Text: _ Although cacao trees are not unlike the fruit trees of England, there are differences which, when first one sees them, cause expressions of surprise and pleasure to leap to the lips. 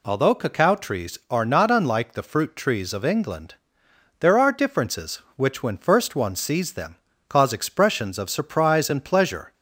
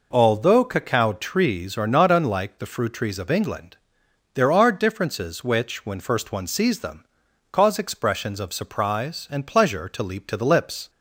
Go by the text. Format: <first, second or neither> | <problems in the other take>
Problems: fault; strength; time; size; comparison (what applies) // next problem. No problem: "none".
second | stops before "to leap to the lips"; at 9.5 s